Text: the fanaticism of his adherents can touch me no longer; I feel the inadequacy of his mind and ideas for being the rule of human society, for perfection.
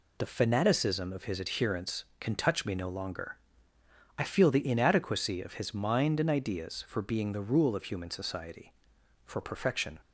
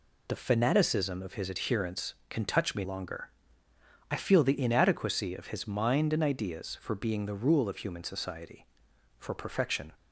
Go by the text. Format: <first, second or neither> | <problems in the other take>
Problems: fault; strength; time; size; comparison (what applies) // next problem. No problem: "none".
first | skips "no"; at 2.8 s